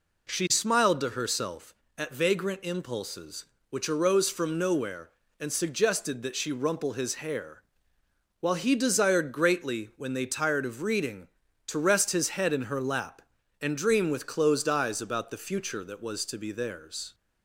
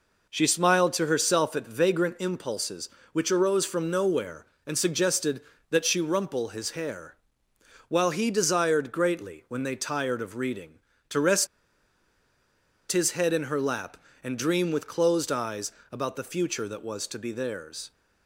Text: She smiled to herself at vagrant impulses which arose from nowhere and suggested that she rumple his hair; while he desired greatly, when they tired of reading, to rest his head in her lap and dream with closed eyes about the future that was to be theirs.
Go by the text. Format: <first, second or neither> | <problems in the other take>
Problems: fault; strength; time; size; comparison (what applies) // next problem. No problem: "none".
first | pauses between "rest" and "his"; strong; at 11.4 s; 1.4 s long // pauses between "eyes" and "about"; slight; at 15.7 s; 0.20 s long